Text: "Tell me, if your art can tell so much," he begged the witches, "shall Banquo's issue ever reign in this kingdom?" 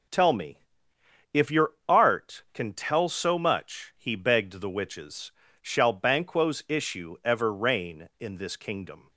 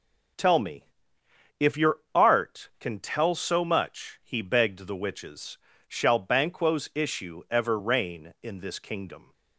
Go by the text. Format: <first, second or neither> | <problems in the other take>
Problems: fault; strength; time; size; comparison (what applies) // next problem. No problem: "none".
neither | none